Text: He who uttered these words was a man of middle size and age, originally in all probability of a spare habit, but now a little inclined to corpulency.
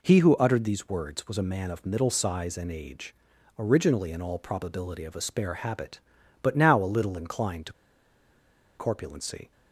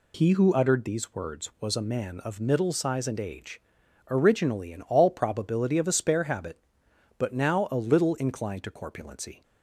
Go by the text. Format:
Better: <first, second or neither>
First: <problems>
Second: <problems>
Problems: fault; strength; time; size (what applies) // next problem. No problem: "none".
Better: second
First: pauses between "to" and "corpulency"; at 7.7 s; 1.0 s long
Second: none